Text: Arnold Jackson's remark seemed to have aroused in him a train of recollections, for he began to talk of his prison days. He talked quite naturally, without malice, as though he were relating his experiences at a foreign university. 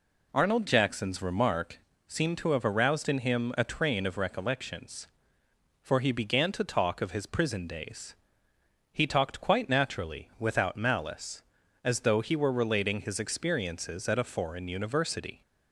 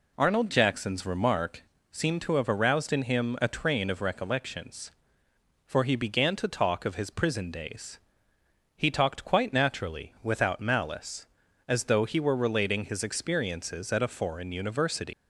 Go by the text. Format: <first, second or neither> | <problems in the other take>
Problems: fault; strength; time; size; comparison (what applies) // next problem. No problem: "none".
first | pauses between "remark" and "seemed"; slight; at 1.6 s; 0.28 s long; slight in the first // leaves "university" unfinished; at 15.1 s; 120 ms